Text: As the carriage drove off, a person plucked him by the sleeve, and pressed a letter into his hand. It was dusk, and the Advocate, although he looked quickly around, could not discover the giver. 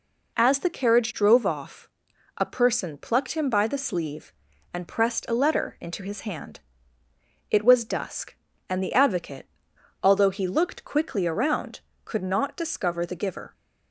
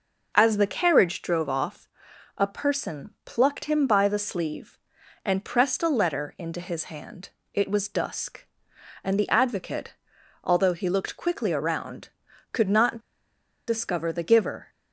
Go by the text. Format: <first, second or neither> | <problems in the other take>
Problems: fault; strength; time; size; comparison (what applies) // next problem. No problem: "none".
first | pauses between "not" and "discover"; noticeable; at 12.9 s; 0.69 s long